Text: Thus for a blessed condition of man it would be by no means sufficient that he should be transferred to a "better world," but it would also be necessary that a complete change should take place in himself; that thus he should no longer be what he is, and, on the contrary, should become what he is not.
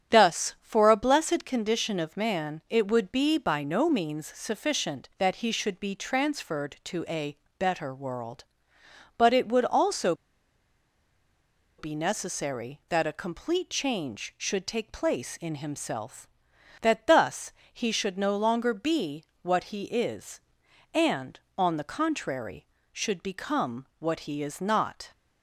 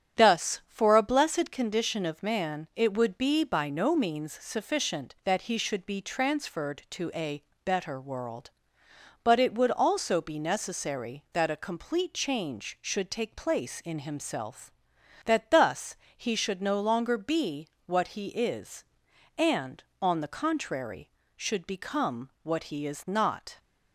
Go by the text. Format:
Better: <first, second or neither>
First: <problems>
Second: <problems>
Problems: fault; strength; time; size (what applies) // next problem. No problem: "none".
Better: second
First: starts louder than the rest; strong; until 1.2 s; 8.5 dB // pauses between "a" and "better"; slight; at 7.3 s; 0.22 s long // pauses between "also" and "be"; strong; at 10.1 s; 1.6 s long // pauses between "thus" and "he"; slight; at 17.5 s; 0.22 s long // pauses between "be" and "what"; slight; at 19.2 s; 0.16 s long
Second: starts louder than the rest; strong; until 1.2 s; 8.5 dB // pauses between "a" and "better"; slight; at 7.4 s; 0.22 s long // pauses between "thus" and "he"; slight; at 15.9 s; 0.22 s long // pauses between "be" and "what"; slight; at 17.6 s; 0.16 s long